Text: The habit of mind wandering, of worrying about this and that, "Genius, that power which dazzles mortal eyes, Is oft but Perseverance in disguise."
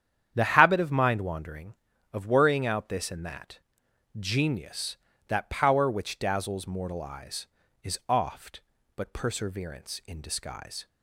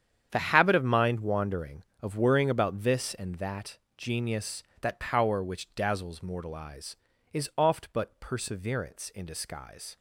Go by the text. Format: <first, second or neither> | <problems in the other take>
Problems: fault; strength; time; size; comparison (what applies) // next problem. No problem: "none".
second | starts louder than the rest; strong; until 1.3 s; 9 dB; strong in the second // says "out" for "about"; at 2.6 s